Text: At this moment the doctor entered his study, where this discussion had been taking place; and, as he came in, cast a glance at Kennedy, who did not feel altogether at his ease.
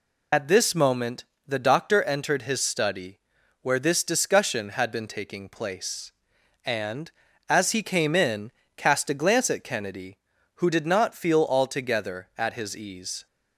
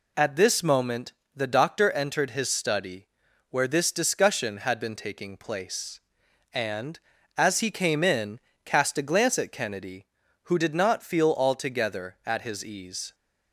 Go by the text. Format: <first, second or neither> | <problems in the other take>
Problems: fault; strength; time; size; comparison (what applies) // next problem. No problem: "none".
second | loses the start of "At"; at 0.3 s; 45 ms // pauses between "moment" and "the"; slight; at 1.2 s; 0.22 s long; slight in the second